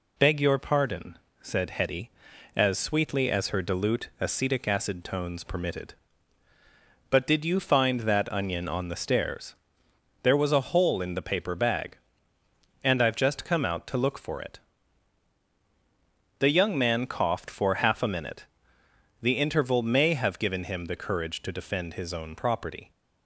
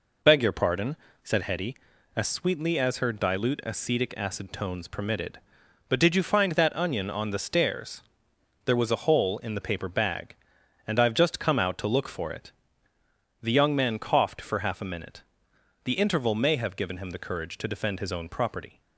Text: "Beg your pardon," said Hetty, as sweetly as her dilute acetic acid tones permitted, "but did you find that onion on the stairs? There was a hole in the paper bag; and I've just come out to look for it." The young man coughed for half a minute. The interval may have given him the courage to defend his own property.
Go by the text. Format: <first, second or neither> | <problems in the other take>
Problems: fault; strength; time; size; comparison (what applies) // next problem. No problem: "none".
neither | none